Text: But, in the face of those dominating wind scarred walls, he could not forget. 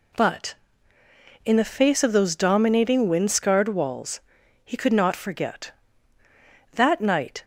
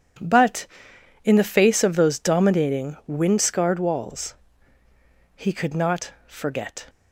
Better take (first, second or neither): second